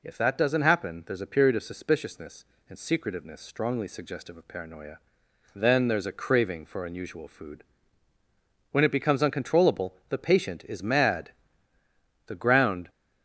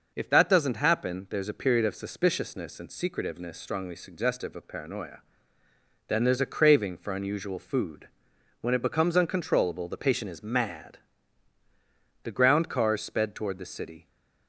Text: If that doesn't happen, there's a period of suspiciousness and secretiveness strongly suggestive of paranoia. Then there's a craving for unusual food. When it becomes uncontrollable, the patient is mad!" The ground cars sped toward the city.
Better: second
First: stops before "cars sped toward the city"; at 12.8 s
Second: none

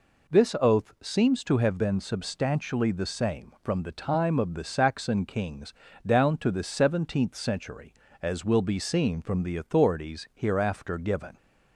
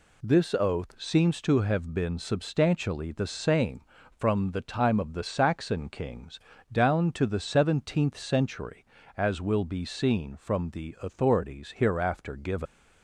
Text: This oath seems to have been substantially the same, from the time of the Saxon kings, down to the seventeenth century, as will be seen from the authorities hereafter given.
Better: first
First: none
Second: leaves "given" unfinished; at 12.6 s; 90 ms

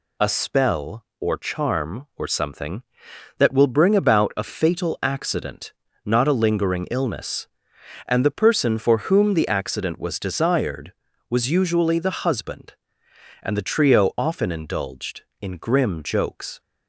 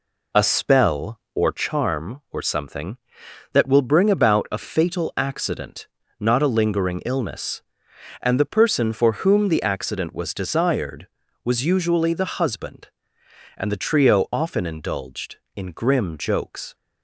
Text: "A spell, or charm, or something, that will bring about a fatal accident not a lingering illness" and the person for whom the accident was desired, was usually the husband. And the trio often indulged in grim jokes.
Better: first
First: pauses between "accident" and "not"; slight; at 5.7 s; 0.32 s long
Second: starts louder than the rest; slight; until 1.9 s; 3 dB // pauses between "accident" and "not"; slight; at 5.8 s; 0.32 s long

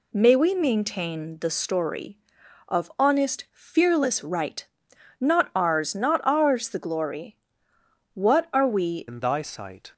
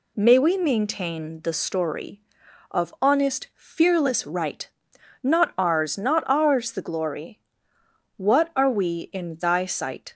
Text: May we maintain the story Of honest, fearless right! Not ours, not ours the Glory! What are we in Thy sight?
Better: second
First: changes voice at "in"; from 9.0 s on; 0.9 s long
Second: none

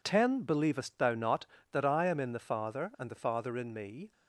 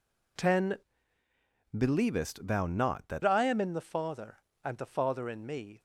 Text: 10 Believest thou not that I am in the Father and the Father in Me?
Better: first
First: none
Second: changes voice from "Believest" to "that"; from 1.7 to 3.2 s; 1.5 s long

